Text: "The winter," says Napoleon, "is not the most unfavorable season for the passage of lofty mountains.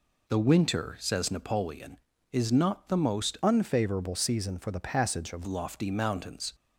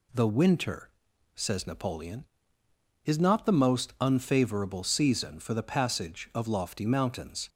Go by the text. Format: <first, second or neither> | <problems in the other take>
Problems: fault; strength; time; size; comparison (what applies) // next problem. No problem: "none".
second | changes voice from "unfavorable" to "of"; from 3.4 to 5.4 s; 2.0 s long